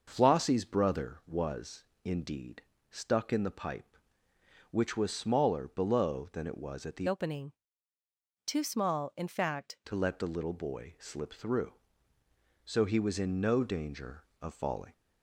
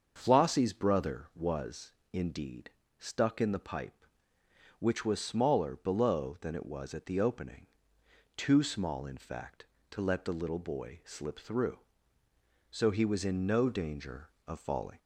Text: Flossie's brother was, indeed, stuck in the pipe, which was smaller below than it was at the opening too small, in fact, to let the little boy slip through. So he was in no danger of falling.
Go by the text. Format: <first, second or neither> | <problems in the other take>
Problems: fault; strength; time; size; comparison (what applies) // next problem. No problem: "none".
second | starts louder than the rest; noticeable; until 1.0 s; 6 dB; also in the second // changes voice from "opening" to "fact"; from 7.0 to 9.7 s; 2.7 s long // pauses between "opening" and "too"; noticeable; at 7.5 s; 0.94 s long; noticeable in the second